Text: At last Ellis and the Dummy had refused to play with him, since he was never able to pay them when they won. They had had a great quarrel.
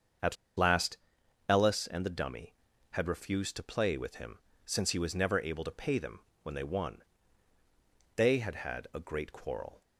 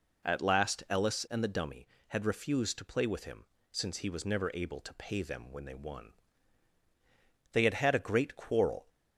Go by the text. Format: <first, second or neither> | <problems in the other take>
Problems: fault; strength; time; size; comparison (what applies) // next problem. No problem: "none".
second | starts louder than the rest; until 1.9 s; 7 dB // pauses between "At" and "last"; slight; at 0.3 s; 0.21 s long // pauses between "last" and "Ellis"; noticeable; at 0.9 s; 0.50 s long // pauses between "them" and "when"; slight; at 6.2 s; 0.22 s long